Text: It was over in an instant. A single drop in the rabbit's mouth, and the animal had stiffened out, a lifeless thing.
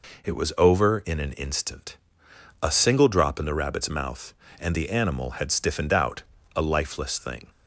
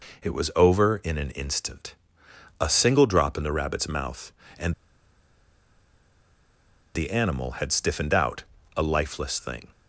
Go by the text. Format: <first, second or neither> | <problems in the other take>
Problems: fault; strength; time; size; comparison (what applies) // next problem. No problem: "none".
first | pauses between "and" and "the"; strong; at 4.7 s; 2.2 s long